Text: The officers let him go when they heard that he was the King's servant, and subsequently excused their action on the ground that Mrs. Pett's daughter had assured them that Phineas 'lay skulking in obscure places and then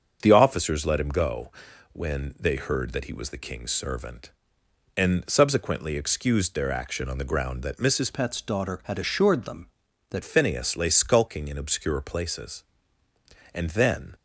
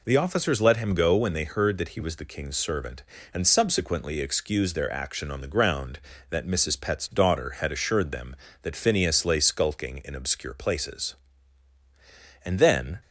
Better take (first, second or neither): second